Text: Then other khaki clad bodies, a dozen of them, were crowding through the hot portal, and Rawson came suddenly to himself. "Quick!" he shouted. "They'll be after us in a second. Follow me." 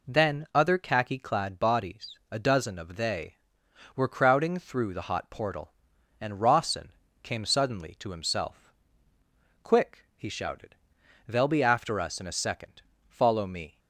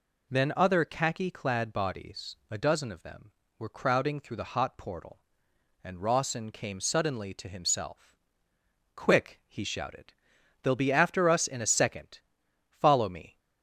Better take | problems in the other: second | says "they" for "them"; at 2.9 s // pauses between "Rawson" and "came"; slight; at 6.9 s; 0.32 s long

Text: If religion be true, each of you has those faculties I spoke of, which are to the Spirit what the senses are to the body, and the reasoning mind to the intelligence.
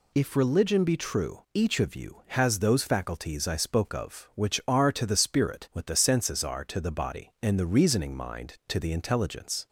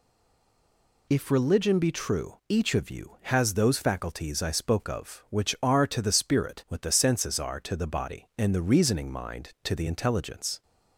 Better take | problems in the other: first | stays silent before the first word; until 1.0 s; 1.0 s long

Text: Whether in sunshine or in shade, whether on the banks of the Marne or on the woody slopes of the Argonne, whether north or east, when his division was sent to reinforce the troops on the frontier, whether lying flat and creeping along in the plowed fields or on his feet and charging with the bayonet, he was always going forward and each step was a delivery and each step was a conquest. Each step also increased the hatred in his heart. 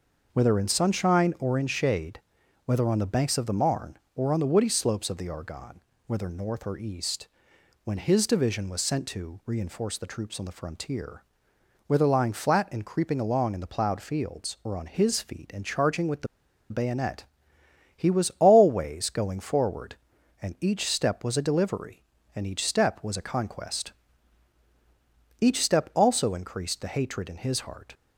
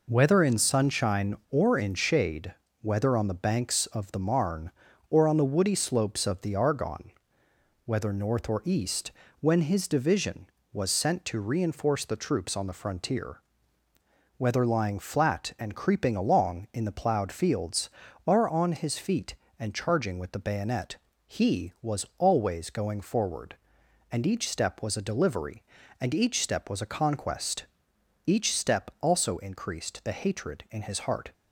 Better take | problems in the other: second | pauses between "the" and "bayonet"; at 16.2 s; 0.44 s long

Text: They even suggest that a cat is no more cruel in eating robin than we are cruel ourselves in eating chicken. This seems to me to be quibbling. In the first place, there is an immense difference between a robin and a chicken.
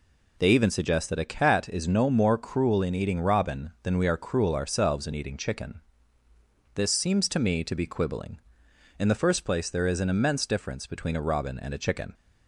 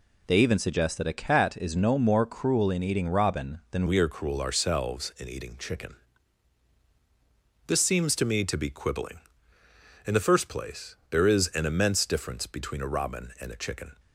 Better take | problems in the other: first | changes voice at "we"; from 3.8 s on; 10.1 s long

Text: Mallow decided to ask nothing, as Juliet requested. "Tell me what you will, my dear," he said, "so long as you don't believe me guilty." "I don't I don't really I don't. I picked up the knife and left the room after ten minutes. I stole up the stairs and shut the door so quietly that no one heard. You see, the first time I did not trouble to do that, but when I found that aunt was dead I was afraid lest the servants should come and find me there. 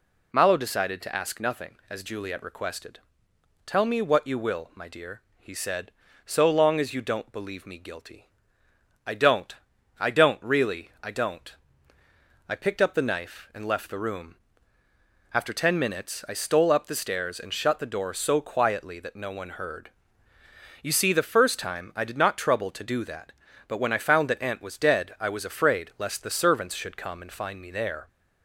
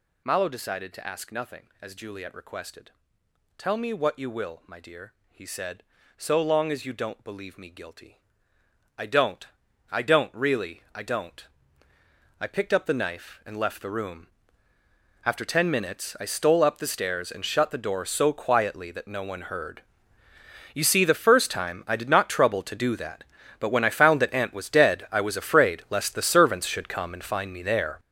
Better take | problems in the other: first | gets louder; strong; throughout; 12 dB // pauses between "don't" and "I"; at 9.4 s; 0.44 s long; also in the first // pauses between "room" and "after"; noticeable; at 14.2 s; 0.98 s long; noticeable in the first

